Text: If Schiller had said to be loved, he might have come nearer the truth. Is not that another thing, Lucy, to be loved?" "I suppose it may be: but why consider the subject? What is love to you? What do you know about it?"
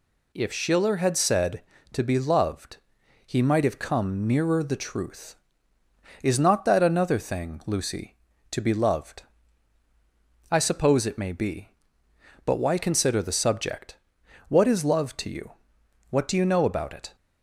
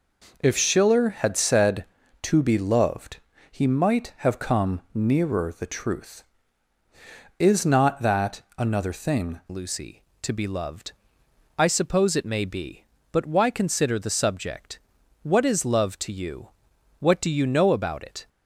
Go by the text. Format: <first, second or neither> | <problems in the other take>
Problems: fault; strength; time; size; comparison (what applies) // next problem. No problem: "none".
first | pauses between "that" and "another"; slight; at 8.4 s; 0.16 s long // changes voice at "Lucy"; from 9.5 s on; 8.7 s long